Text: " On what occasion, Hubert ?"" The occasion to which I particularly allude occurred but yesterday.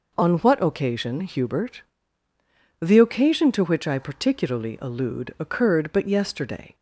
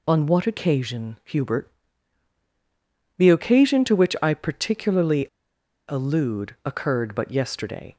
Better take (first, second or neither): first